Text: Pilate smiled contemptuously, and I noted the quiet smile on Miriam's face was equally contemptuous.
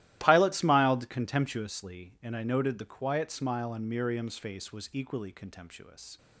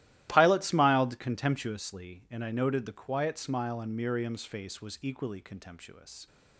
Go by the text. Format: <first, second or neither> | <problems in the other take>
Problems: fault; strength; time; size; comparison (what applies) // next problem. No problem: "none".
neither | starts louder than the rest; strong; the same in both